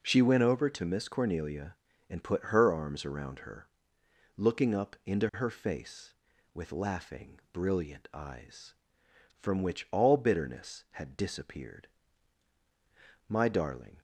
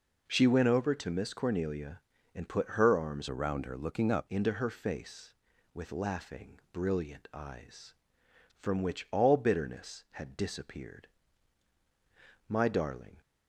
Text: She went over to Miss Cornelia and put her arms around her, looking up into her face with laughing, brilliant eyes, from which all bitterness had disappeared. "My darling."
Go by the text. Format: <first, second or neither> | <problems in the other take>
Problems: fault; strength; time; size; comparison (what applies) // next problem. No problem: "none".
first | changes voice from "around" to "up"; from 3.2 to 4.2 s; 1.0 s long